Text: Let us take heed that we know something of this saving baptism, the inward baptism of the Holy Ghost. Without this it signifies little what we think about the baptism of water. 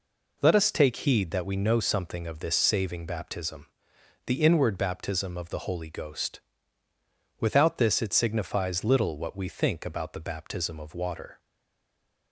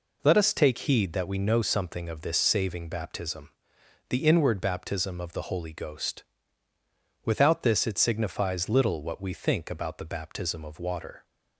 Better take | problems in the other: second | stays silent after the last word; slight; from 11.3 s on; 1.0 s long

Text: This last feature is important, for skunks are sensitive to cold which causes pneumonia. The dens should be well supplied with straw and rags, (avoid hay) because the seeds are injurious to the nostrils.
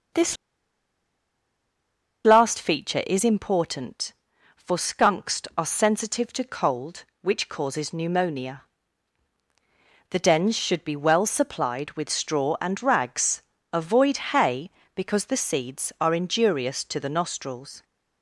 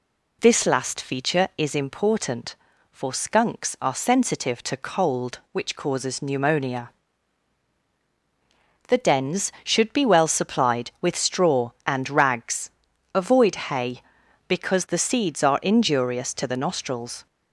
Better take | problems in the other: second | starts louder than the rest; noticeable; until 3.0 s; 6 dB // pauses between "This" and "last"; strong; at 0.3 s; 1.8 s long

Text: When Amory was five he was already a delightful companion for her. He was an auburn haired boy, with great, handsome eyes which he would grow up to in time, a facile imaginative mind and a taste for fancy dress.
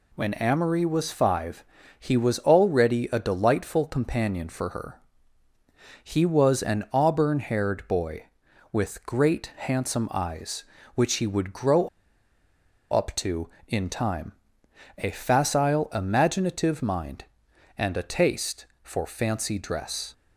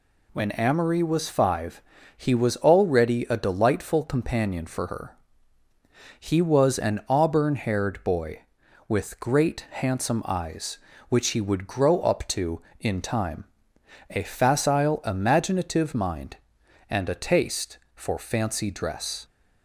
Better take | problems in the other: second | pauses between "five" and "he"; slight; at 1.6 s; 0.34 s long; slight in the second // pauses between "grow" and "up"; at 11.8 s; 1.0 s long

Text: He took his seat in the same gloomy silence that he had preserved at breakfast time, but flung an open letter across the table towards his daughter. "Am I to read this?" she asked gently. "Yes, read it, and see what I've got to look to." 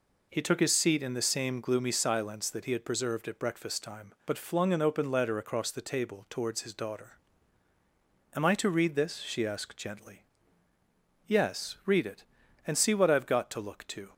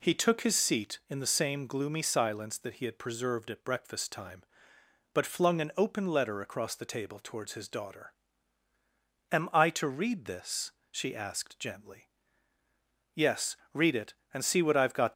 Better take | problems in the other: first | stops before "to look to"; at 15.1 s

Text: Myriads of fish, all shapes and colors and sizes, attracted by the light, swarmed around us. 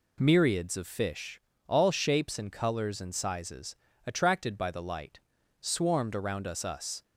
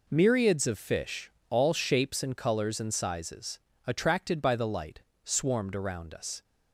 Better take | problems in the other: second | says "us" twice; at 6.6 s

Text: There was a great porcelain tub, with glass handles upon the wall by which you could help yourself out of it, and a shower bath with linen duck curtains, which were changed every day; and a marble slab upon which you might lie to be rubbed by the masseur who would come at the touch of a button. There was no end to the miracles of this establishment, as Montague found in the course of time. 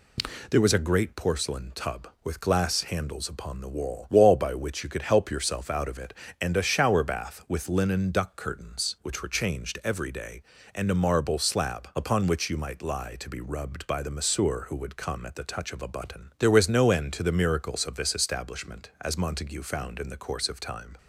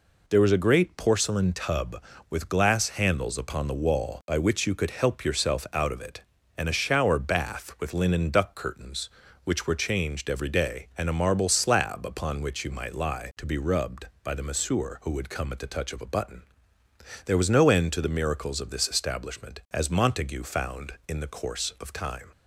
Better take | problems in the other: second | says "wall" twice; at 4.1 s

